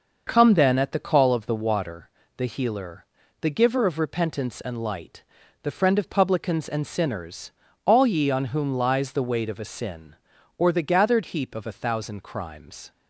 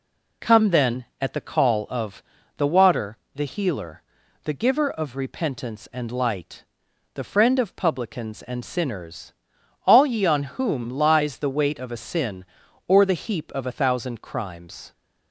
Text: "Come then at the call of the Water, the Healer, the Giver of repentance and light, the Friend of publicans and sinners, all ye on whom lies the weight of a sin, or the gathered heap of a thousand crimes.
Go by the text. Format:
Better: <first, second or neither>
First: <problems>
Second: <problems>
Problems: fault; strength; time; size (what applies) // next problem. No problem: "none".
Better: first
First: none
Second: pauses between "of" and "the"; slight; at 2.2 s; 0.36 s long // skips "gathered"; at 13.1 s